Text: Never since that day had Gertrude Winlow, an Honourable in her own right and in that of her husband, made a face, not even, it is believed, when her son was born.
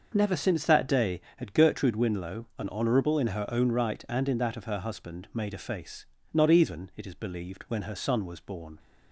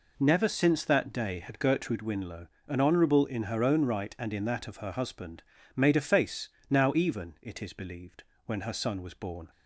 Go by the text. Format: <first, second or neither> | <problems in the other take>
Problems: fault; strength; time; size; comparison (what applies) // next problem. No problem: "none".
first | says "now" for "not"; at 6.6 s